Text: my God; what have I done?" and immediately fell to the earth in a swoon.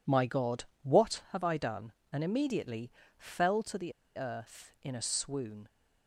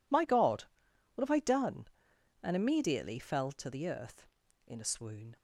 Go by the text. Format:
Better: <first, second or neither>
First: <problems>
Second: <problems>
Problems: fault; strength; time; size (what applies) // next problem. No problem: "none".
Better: second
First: pauses between "immediately" and "fell"; slight; at 2.9 s; 0.26 s long // pauses between "the" and "earth"; slight; at 3.9 s; 0.25 s long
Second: none